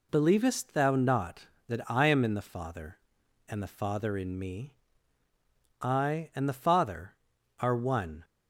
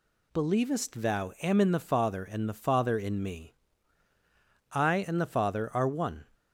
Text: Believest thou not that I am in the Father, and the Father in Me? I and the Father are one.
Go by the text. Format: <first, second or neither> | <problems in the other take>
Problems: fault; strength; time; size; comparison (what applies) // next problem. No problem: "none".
first | skips "not that I"; at 1.3 s